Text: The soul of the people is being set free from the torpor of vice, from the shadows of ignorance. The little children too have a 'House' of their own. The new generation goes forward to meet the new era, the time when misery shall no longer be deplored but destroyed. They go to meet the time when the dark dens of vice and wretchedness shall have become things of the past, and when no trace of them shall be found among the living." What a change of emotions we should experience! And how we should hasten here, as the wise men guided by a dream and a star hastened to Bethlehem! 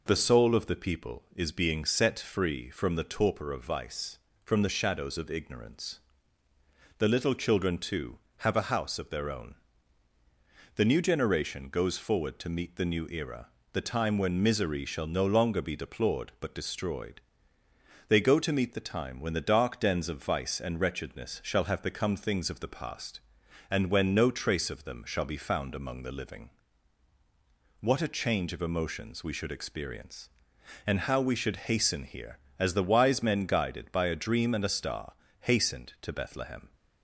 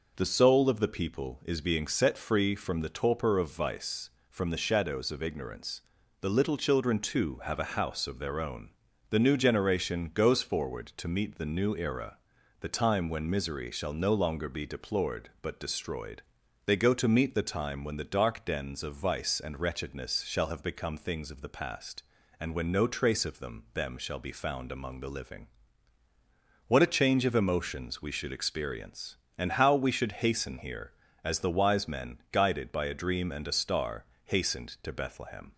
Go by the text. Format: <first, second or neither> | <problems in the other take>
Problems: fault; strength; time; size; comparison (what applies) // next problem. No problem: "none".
first | says "them" twice; at 23.7 s // pauses between "star" and "hastened"; slight; at 34.0 s; 0.20 s long; slight in the first